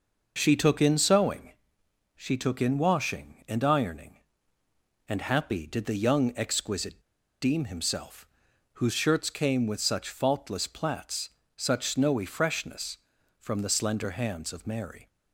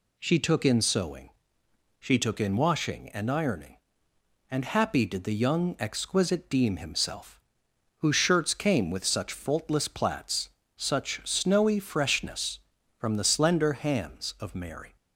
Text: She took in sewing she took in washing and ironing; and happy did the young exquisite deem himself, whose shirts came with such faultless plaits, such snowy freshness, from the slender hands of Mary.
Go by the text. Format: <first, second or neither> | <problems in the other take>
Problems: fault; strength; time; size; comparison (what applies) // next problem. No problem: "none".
second | pauses between "sewing" and "she"; noticeable; at 1.5 s; 0.62 s long; noticeable in the second // pauses between "exquisite" and "deem"; at 7.0 s; 0.40 s long